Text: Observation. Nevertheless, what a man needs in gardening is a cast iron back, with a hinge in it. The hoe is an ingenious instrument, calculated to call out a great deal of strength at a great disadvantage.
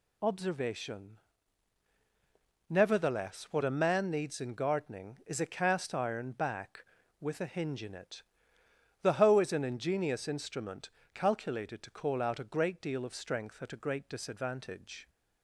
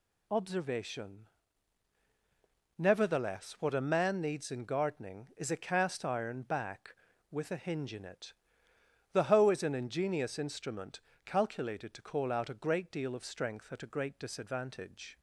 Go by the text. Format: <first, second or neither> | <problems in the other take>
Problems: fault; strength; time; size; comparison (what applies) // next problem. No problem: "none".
neither | none